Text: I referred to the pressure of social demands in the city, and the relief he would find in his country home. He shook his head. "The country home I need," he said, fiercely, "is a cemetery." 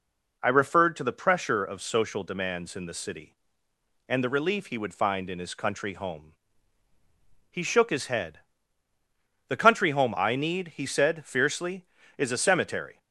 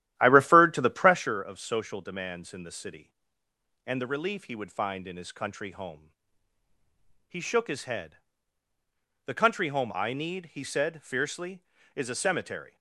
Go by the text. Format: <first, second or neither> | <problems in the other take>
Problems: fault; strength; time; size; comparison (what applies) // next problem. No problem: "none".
first | starts louder than the rest; strong; until 1.3 s; 12.5 dB